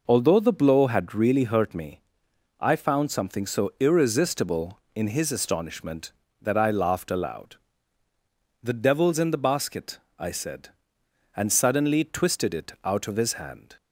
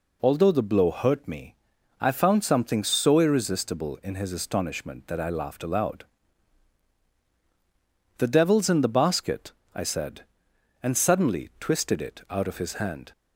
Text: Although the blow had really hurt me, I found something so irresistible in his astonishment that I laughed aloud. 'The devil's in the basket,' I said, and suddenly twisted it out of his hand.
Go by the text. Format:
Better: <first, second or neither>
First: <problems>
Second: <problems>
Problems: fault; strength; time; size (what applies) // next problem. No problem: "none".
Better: first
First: none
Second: skips "had really"; at 0.8 s